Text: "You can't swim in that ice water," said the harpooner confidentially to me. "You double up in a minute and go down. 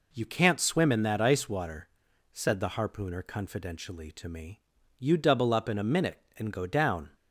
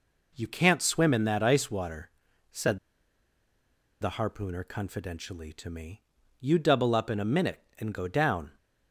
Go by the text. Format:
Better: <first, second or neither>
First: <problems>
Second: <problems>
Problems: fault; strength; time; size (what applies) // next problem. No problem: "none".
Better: first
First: none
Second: pauses between "said" and "the"; at 2.7 s; 1.2 s long